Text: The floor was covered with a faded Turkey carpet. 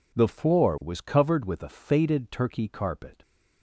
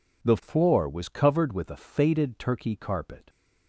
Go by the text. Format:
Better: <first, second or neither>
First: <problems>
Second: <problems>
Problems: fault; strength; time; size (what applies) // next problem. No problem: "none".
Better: neither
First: none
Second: none